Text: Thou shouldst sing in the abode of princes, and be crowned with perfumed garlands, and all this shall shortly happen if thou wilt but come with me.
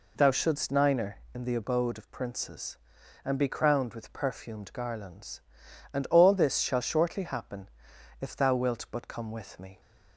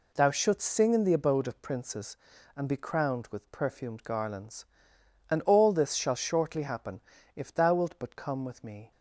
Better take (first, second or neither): second